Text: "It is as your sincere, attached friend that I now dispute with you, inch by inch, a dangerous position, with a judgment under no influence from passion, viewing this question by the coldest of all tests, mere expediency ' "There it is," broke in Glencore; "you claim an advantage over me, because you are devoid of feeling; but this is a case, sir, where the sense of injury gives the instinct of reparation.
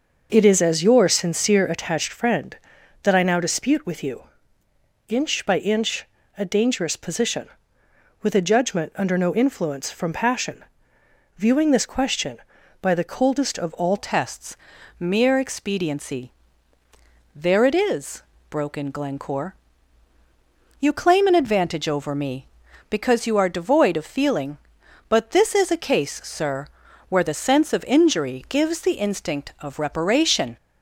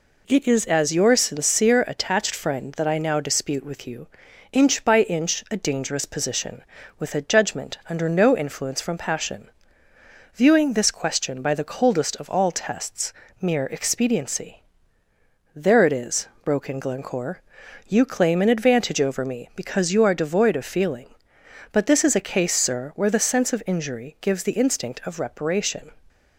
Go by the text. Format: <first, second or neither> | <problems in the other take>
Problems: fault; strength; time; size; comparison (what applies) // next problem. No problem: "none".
second | starts louder than the rest; until 1.3 s; 6 dB // changes voice at "tests"; from 13.9 s on; 16.6 s long